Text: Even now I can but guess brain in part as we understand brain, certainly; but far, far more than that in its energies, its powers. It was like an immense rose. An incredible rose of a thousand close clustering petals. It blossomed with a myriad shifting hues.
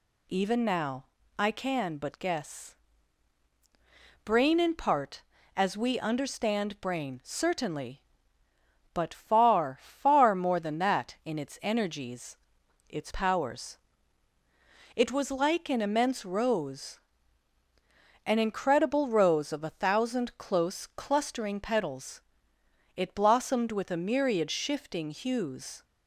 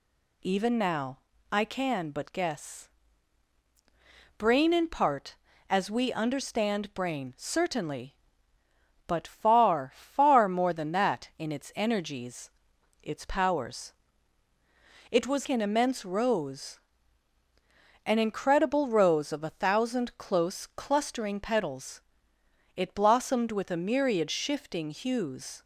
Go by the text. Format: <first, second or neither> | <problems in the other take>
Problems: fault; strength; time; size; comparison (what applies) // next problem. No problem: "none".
first | pauses between "now" and "I"; slight; at 1.1 s; 0.32 s long; slight in the first // pauses between "guess" and "brain"; strong; at 2.8 s; 1.4 s long; strong in the first // skips "like"; at 15.4 s